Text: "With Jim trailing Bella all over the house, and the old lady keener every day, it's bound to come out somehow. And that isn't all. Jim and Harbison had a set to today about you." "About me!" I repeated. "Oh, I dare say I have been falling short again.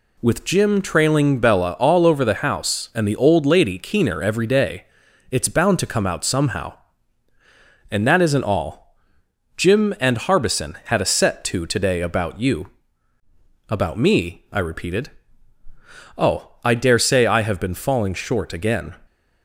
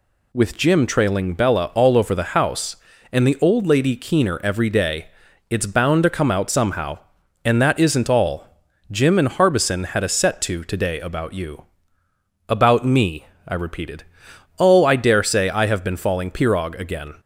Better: first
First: none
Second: says "pirog" for "short"; at 16.2 s

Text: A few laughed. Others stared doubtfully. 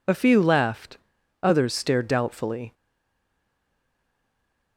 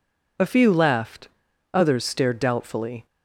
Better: second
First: stays silent after the last word; noticeable; from 2.7 s on; 2.0 s long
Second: none

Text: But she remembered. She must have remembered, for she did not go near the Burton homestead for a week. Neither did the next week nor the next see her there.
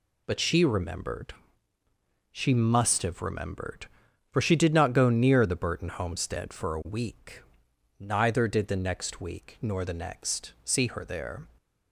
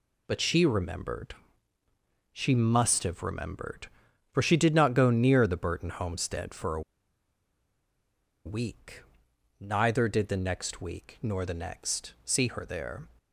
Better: first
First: none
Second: pauses between "a" and "week"; strong; at 6.8 s; 1.6 s long

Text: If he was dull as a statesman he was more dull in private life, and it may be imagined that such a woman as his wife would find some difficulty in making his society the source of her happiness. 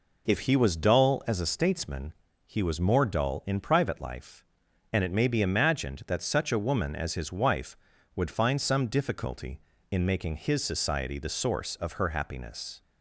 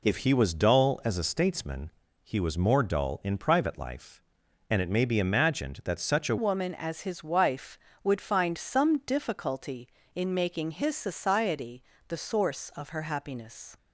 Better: first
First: pauses between "statesman" and "he"; slight; at 2.1 s; 0.32 s long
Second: pauses between "statesman" and "he"; slight; at 1.8 s; 0.32 s long // changes voice at "woman"; from 6.3 s on; 7.4 s long // pauses between "society" and "the"; slight; at 11.8 s; 0.26 s long

